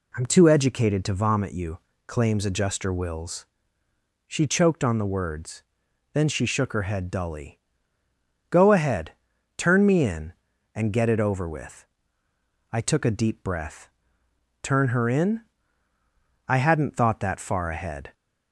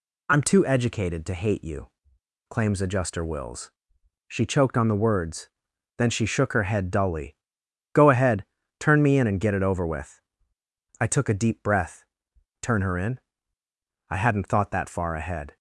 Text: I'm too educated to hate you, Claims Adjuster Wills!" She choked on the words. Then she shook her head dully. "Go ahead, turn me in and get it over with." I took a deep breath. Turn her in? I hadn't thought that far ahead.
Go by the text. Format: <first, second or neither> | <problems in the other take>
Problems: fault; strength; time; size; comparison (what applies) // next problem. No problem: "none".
second | says "vomit" for "hate"; at 1.1 s